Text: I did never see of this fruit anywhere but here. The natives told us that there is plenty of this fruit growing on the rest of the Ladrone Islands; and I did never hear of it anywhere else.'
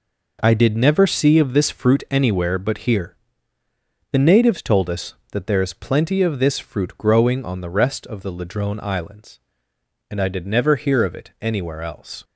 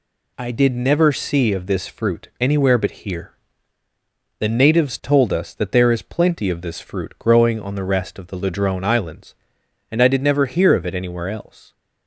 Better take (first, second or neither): neither